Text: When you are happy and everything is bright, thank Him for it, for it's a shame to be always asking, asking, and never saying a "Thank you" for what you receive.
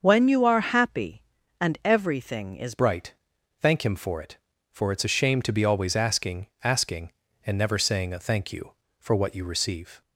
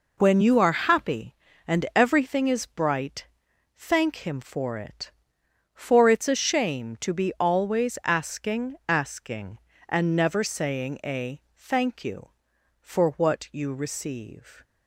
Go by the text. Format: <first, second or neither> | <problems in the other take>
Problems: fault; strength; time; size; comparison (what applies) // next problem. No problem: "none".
second | starts louder than the rest; until 1.0 s; 6.5 dB // changes voice at "bright"; from 2.7 s on; 7.3 s long